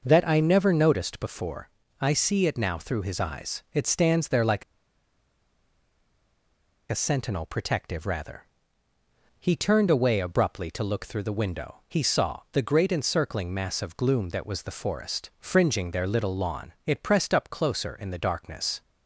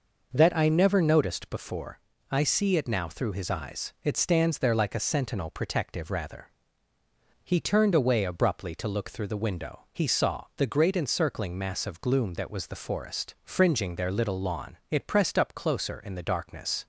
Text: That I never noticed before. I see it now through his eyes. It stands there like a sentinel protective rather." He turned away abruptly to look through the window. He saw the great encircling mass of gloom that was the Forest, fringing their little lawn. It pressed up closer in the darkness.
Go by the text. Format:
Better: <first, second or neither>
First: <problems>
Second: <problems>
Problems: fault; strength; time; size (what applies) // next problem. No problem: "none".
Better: second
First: pauses between "like" and "a"; strong; at 4.6 s; 2.2 s long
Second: none